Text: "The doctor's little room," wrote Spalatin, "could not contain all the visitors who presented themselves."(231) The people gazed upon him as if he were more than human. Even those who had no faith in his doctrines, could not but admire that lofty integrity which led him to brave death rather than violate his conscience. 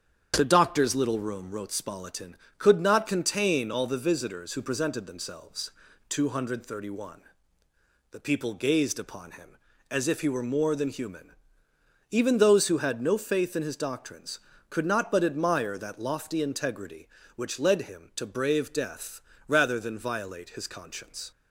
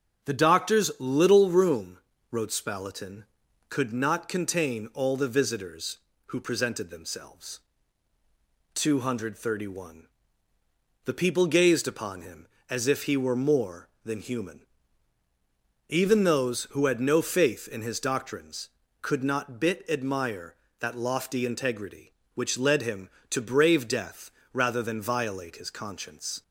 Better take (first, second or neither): first